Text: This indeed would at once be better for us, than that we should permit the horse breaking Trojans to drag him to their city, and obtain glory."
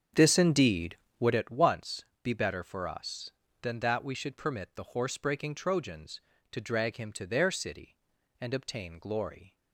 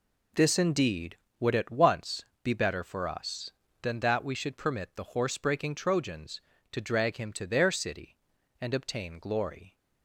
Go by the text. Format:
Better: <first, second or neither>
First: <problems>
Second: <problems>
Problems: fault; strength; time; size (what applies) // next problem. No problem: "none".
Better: second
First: starts louder than the rest; strong; until 1.5 s; 7.5 dB // pauses between "once" and "be"; slight; at 2.0 s; 0.20 s long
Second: pauses between "once" and "be"; slight; at 2.2 s; 0.20 s long